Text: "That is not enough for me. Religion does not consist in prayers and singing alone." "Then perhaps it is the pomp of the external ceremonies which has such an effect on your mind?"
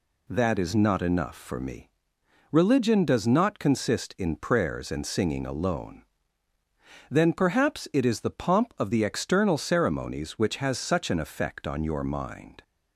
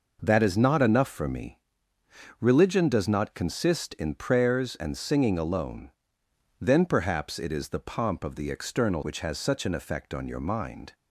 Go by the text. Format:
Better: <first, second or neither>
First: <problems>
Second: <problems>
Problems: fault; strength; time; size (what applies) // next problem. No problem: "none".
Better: first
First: none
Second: skips "ceremonies"; at 9.0 s